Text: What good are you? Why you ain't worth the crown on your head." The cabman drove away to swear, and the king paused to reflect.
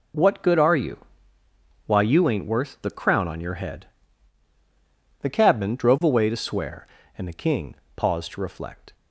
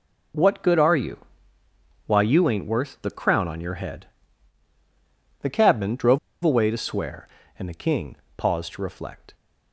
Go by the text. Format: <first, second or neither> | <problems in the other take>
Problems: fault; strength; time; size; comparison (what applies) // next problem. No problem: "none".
first | pauses between "drove" and "away"; slight; at 6.1 s; 0.24 s long // pauses between "king" and "paused"; slight; at 8.1 s; 0.18 s long; slight in the first